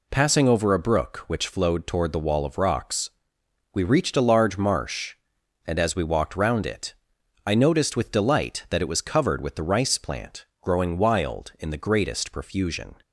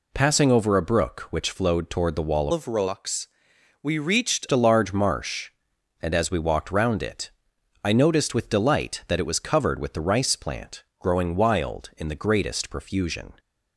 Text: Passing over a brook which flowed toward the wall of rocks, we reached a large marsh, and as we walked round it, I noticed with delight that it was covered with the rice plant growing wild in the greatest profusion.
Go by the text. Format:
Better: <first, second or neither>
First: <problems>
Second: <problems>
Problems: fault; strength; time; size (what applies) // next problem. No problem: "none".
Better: first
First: pauses between "plant" and "growing"; slight; at 10.4 s; 0.16 s long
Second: changes voice from "of" to "reached"; from 2.5 to 4.4 s; 1.9 s long // pauses between "plant" and "growing"; slight; at 10.8 s; 0.16 s long